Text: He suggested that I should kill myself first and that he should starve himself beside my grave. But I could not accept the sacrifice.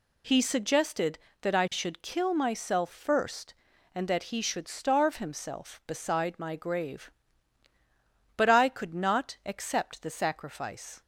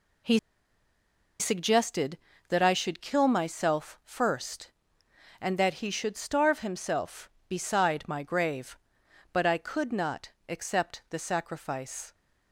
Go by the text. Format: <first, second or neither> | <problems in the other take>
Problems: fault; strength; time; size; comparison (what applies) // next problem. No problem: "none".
first | pauses between "He" and "suggested"; at 0.3 s; 1.0 s long // pauses between "not" and "accept"; slight; at 10.2 s; 0.18 s long